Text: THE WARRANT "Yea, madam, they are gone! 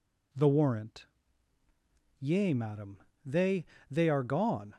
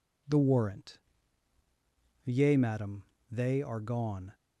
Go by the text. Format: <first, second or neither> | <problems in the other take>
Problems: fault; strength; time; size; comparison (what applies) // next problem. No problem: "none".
second | pauses between "WARRANT" and "Yea"; at 1.0 s; 1.1 s long; also in the second // says "they" twice; at 3.8 s